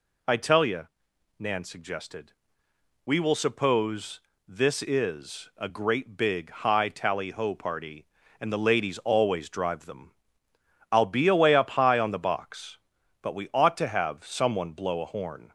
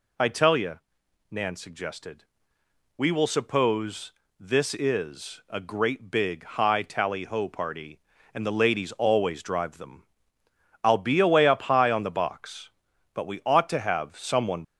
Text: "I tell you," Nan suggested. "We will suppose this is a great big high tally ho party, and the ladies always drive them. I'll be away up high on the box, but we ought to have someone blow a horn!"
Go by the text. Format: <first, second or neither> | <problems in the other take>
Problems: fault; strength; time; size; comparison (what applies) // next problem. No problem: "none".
first | pauses between "suppose" and "this"; slight; at 4.1 s; 0.28 s long; slight in the first // stops before "blow a horn"; at 14.6 s